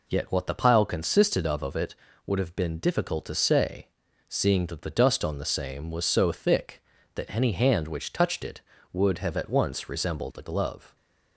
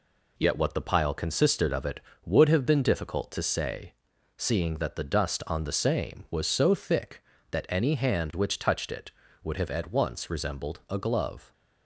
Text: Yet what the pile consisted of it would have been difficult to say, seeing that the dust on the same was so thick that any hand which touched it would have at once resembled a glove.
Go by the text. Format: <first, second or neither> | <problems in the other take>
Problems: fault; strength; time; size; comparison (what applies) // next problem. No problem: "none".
second | says "of" twice; at 1.6 s